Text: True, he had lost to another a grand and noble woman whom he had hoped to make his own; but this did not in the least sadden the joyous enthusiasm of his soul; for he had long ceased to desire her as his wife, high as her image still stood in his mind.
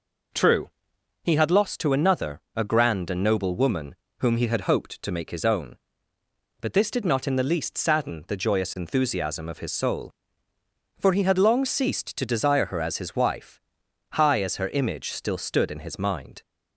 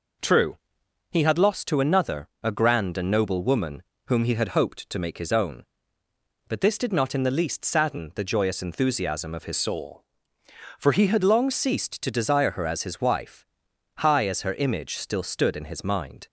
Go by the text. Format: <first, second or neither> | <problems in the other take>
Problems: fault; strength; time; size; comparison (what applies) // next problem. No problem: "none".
first | pauses between "another" and "a"; slight; at 2.2 s; 0.16 s long; slight in the first // pauses between "woman" and "whom"; slight; at 3.8 s; 0.24 s long; slight in the first // changes voice from "soul" to "had"; from 9.5 to 11.2 s; 1.7 s long